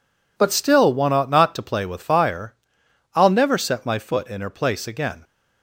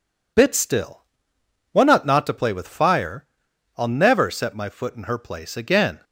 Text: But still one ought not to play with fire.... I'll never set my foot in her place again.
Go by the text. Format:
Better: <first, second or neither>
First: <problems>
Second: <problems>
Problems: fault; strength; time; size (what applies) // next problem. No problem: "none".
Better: first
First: none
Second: says "Bit" for "But"; at 0.3 s // pauses between "still" and "one"; noticeable; at 1.0 s; 0.72 s long